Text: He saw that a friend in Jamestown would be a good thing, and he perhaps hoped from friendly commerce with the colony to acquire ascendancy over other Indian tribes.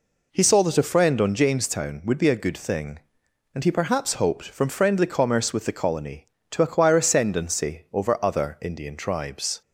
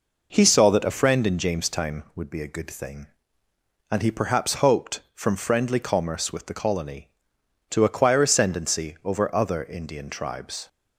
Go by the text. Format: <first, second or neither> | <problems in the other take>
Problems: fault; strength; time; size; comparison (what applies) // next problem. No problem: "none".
second | says "on" for "in"; at 1.2 s